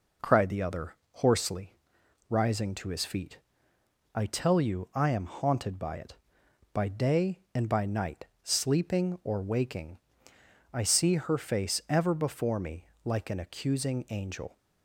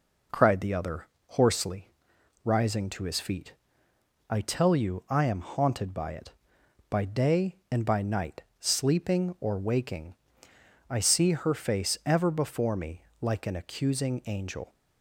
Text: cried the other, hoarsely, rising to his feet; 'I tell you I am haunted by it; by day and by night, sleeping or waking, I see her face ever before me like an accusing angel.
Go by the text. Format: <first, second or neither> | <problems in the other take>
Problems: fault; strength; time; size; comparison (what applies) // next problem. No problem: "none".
neither | pauses between "me" and "like"; slight; the same in both